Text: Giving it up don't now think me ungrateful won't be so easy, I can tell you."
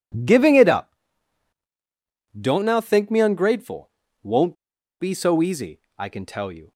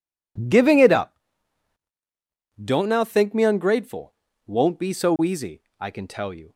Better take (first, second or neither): second